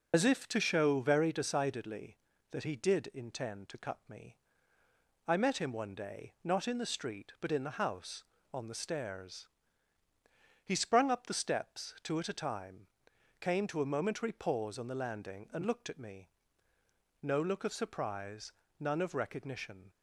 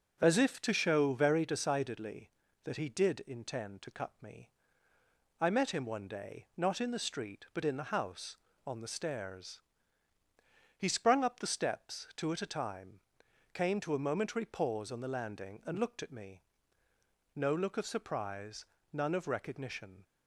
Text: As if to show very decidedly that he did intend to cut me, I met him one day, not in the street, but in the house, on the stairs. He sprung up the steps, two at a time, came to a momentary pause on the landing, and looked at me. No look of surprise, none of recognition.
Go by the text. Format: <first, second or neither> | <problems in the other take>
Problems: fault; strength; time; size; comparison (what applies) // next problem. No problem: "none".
second | loses the start of "As"; at 0.1 s; 70 ms